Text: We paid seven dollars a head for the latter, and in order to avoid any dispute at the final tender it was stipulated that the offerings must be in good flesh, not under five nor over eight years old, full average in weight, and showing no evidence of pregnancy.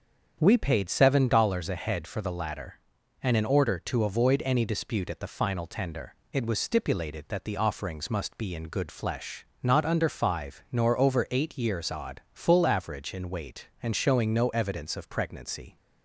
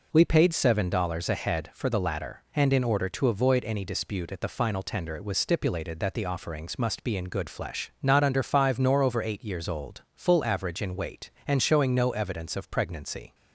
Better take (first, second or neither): second